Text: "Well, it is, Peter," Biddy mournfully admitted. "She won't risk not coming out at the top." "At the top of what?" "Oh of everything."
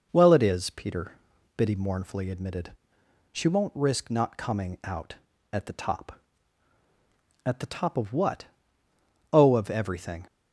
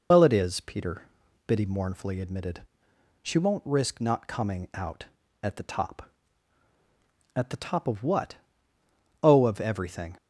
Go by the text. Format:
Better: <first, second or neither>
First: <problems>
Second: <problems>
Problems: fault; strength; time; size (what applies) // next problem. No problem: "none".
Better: first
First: none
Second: loses the start of "Well"; at 0.1 s; 90 ms